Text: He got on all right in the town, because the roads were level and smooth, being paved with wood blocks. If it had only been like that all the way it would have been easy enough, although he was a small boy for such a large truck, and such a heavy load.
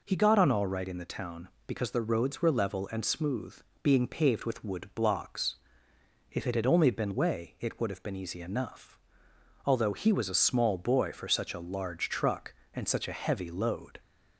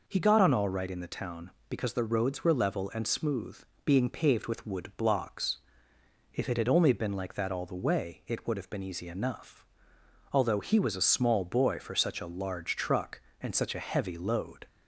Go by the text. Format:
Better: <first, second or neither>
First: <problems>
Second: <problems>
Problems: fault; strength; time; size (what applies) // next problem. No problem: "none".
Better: second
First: skips "like that all the"; at 7.1 s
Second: none